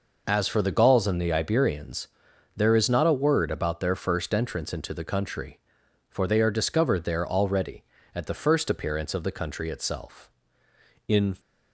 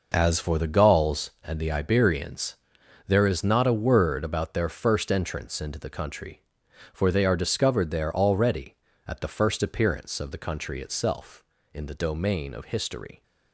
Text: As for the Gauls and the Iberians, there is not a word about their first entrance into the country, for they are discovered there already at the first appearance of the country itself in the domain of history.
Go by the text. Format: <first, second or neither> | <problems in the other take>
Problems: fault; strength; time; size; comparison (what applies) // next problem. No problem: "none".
second | stops before "the domain of history"; at 11.3 s